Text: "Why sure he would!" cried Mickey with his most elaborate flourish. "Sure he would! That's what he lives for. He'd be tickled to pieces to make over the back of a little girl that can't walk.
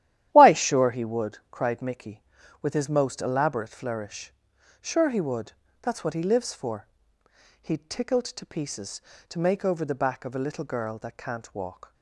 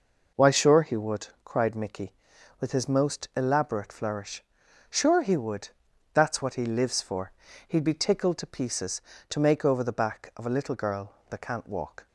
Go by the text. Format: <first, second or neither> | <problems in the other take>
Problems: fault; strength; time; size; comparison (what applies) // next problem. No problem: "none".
second | starts louder than the rest; strong; until 1.3 s; 12 dB // skips "be"; at 7.8 s